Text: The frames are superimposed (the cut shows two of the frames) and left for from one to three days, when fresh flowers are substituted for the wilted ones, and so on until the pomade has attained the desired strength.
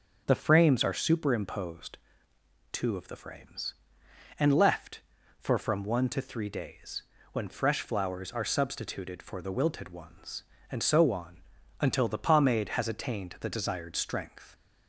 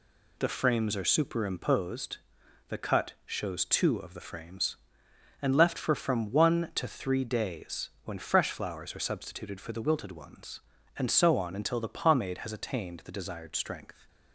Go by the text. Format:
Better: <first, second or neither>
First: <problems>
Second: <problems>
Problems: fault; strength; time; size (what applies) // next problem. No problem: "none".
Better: second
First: starts louder than the rest; until 1.2 s; 6.5 dB // skips "the cut shows"; at 2.3 s // pauses between "on" and "until"; at 11.4 s; 0.38 s long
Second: none